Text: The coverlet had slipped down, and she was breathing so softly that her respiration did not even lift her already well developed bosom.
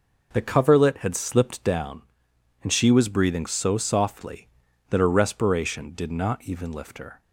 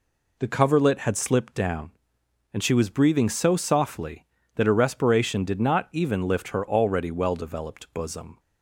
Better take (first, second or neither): second